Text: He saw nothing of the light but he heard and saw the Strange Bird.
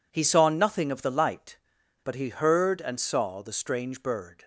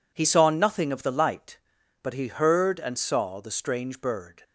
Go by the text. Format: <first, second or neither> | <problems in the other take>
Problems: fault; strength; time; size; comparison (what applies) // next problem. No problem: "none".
neither | none